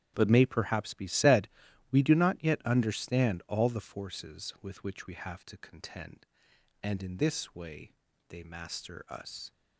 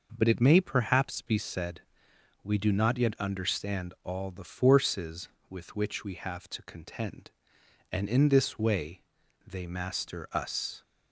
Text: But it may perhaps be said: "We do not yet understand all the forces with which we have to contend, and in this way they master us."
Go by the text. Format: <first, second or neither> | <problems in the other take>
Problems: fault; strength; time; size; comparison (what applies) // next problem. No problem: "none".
second | starts louder than the rest; strong; until 1.1 s; 10.5 dB // skips "it"; at 0.2 s // pauses between "way" and "they"; at 7.9 s; 0.38 s long; also in the second